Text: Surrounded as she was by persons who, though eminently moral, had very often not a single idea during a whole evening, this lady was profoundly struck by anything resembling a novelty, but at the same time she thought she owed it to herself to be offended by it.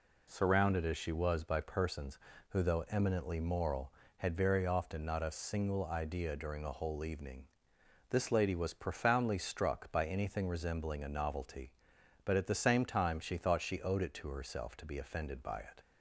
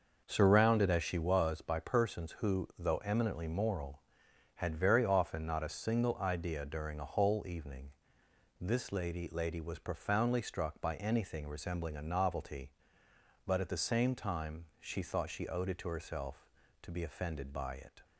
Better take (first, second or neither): first